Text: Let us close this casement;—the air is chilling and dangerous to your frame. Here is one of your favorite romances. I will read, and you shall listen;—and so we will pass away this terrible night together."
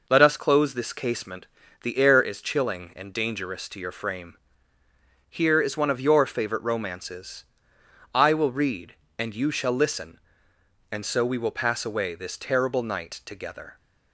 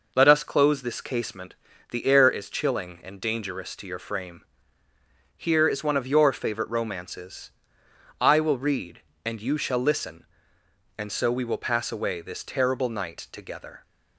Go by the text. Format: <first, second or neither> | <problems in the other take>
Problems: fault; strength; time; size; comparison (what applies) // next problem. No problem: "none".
neither | none